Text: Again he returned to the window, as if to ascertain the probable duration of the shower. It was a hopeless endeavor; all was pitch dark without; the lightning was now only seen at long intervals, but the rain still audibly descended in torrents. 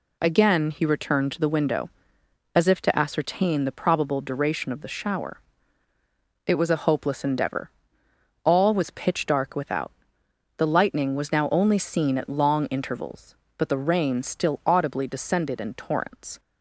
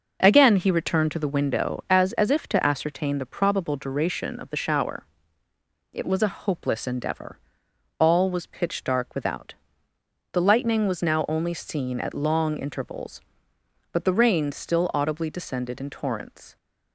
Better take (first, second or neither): first